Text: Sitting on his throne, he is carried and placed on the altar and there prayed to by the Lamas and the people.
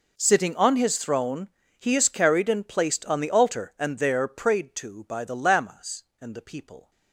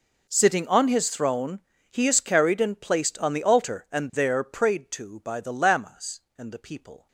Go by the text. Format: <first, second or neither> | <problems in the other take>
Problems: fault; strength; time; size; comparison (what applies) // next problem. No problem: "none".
neither | none